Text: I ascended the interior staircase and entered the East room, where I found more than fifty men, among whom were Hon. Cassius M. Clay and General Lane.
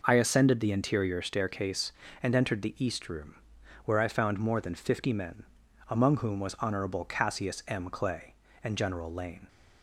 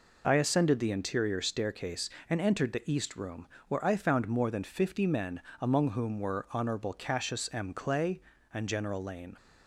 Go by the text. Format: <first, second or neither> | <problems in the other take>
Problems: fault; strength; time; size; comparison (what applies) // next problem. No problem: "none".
second | says "was" for "were"; at 6.3 s